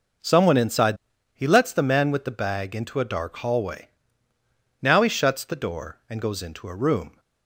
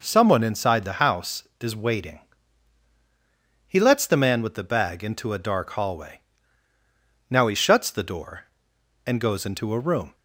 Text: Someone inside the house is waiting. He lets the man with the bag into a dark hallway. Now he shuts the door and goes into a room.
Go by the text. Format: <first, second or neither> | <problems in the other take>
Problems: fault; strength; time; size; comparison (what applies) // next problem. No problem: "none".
second | skips "the house is waiting"; at 1.1 s